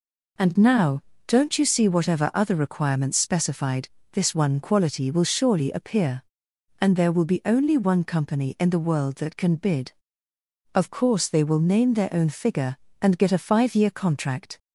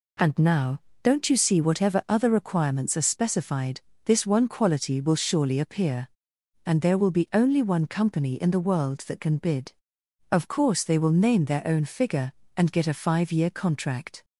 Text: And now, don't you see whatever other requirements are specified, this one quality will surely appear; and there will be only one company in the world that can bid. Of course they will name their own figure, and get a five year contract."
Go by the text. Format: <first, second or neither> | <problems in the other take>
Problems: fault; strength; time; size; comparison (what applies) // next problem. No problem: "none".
second | skips "are"; at 3.1 s